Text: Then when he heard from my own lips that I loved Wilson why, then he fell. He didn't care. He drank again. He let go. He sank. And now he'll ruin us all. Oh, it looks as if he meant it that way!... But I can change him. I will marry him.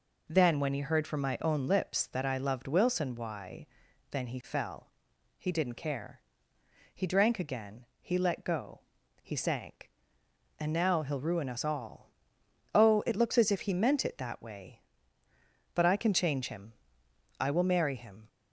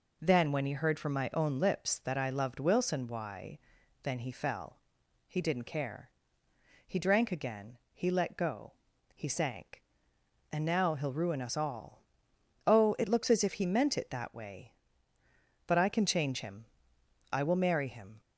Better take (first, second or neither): neither